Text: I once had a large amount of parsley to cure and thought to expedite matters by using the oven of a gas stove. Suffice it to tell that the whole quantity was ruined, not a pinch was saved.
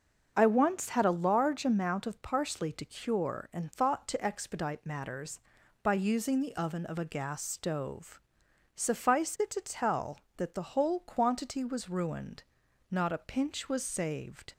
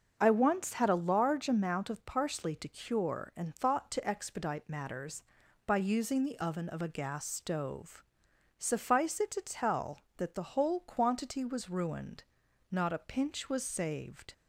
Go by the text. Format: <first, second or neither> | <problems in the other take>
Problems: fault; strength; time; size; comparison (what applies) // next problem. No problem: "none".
neither | starts louder than the rest; the same in both